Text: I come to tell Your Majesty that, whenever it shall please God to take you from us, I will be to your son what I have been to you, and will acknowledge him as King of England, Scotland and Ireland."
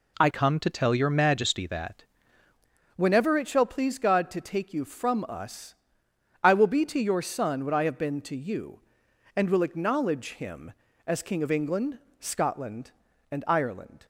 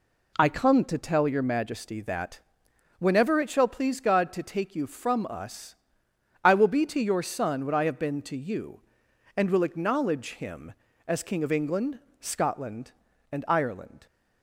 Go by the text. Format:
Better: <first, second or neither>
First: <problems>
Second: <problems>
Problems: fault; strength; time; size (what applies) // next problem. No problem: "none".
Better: second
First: changes voice from "come" to "that"; from 0.3 to 2.0 s; 1.7 s long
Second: none